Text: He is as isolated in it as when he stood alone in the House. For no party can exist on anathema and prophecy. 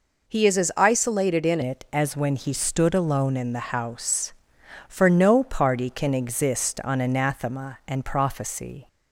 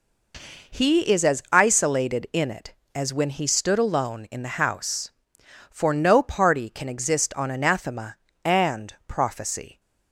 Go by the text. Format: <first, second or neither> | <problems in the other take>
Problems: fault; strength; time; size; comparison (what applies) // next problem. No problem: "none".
second | changes voice at "it"; from 1.6 s on; 7.2 s long